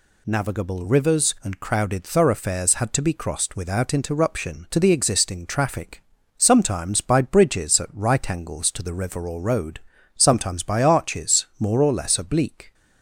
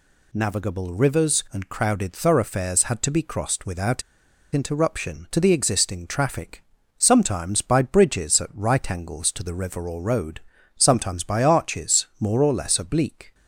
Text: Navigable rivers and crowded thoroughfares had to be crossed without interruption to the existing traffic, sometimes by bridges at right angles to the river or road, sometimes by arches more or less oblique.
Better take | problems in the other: first | pauses between "without" and "interruption"; noticeable; at 4.0 s; 0.52 s long

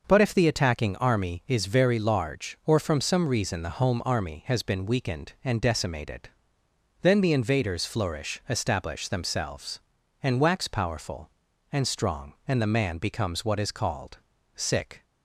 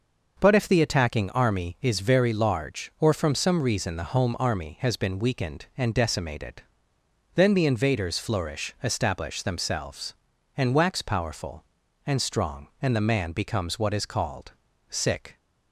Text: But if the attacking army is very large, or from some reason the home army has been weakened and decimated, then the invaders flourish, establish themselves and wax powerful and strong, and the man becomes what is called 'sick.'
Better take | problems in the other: neither | pauses between "called" and "sick"; slight; the same in both

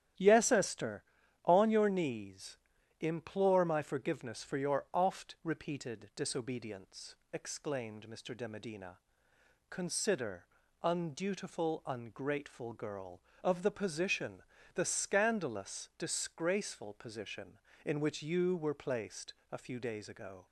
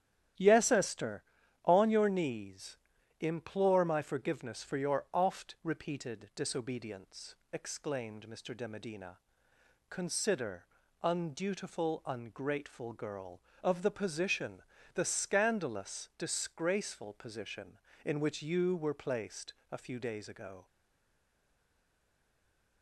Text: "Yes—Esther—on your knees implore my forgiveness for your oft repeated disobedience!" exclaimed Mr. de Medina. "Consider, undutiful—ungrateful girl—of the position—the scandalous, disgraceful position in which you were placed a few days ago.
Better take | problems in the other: first | starts louder than the rest; strong; until 1.7 s; 11 dB; strong in the first // pauses between "knees" and "implore"; noticeable; at 2.7 s; 0.46 s long; noticeable in the first // pauses between "placed" and "a"; slight; at 19.5 s; 0.18 s long; slight in the first // stays silent after the last word; from 20.6 s on; 2.2 s long

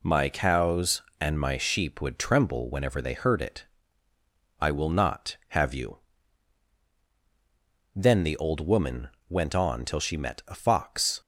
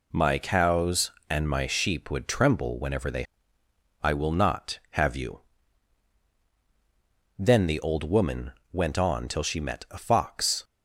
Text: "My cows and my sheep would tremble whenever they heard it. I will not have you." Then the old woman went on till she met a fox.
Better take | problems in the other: first | skips "heard it"; at 3.6 s // pauses between "woman" and "went"; slight; at 8.5 s; 0.20 s long; slight in the first

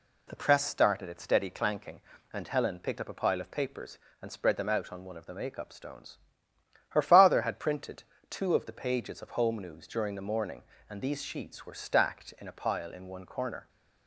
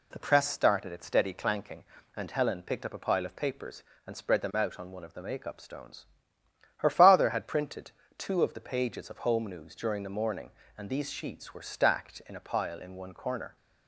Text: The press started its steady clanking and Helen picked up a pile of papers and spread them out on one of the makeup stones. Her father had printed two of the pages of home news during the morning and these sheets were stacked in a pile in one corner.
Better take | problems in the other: neither | pauses between "printed" and "two"; slight; the same in both

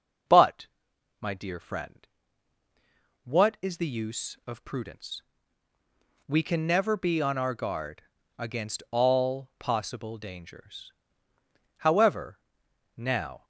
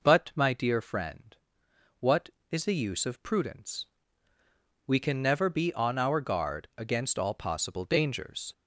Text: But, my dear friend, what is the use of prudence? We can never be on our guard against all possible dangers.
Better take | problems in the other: second | pauses between "guard" and "against"; slight; at 8.0 s; 0.36 s long // goes on to say "However now"; from 11.7 s on; 1.6 s long

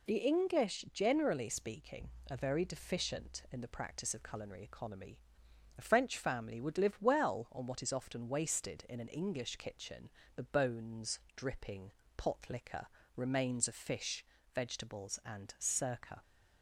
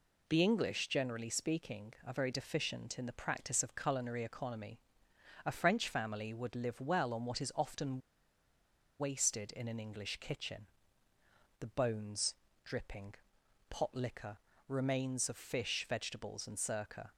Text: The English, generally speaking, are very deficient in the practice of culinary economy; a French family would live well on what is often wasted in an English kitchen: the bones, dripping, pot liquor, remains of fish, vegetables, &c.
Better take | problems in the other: first | pauses between "often" and "wasted"; at 8.0 s; 0.99 s long

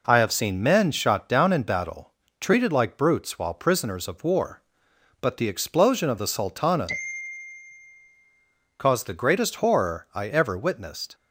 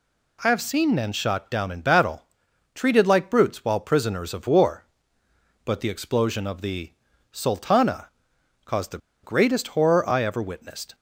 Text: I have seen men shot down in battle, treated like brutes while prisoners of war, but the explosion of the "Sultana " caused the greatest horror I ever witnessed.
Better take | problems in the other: first | pauses between "the" and "Sultana"; at 6.9 s; 0.40 s long // pauses between "the" and "greatest"; slight; at 8.9 s; 0.25 s long

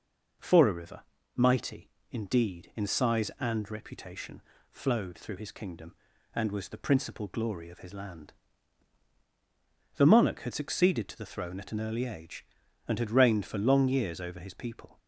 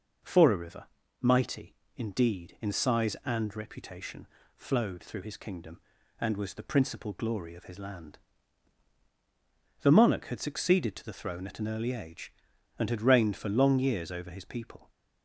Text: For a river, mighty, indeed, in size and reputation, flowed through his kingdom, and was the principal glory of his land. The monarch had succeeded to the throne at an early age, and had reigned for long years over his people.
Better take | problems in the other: neither | none

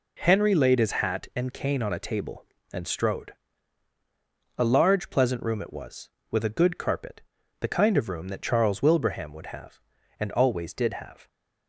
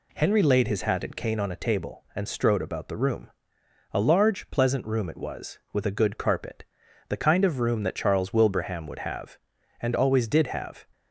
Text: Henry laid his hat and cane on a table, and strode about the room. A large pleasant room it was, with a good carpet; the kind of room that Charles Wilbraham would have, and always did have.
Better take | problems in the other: second | skips "about the room"; at 3.9 s

